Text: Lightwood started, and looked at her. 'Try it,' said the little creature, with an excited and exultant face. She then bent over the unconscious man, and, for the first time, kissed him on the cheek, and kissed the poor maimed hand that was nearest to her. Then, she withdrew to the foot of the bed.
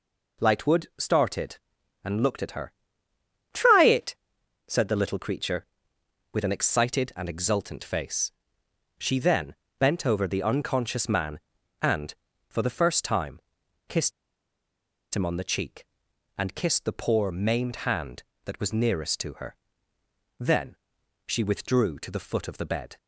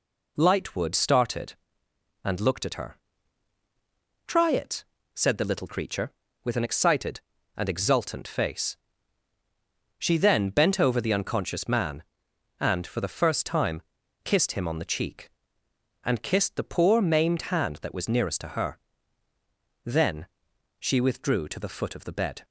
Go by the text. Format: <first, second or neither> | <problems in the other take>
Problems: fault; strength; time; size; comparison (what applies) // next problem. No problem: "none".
second | pauses between "then" and "bent"; slight; at 9.5 s; 0.24 s long // pauses between "kissed" and "him"; at 14.1 s; 1.0 s long